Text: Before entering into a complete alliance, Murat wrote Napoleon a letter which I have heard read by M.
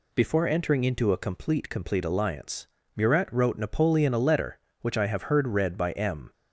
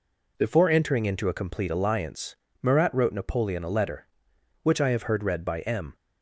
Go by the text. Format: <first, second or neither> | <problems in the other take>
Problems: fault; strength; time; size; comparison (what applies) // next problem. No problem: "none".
second | says "complete" twice; at 1.7 s